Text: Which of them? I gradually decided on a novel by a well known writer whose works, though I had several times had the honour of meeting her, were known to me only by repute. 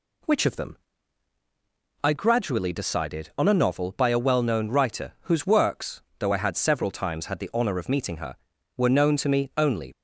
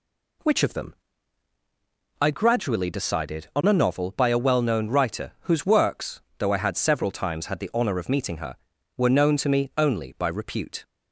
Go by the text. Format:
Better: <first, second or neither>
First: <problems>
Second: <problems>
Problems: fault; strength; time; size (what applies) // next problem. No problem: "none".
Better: second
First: stops before "by repute"; at 9.9 s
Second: none